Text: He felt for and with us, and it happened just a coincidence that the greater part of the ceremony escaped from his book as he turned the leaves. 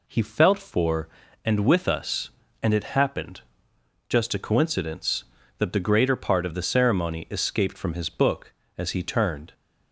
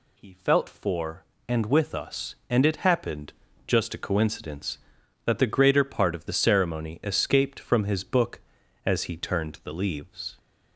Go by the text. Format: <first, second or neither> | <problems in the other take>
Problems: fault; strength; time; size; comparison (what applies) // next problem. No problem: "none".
second | pauses between "happened" and "just"; noticeable; at 3.3 s; 0.68 s long; slight in the second // stops before "the leaves"; at 9.5 s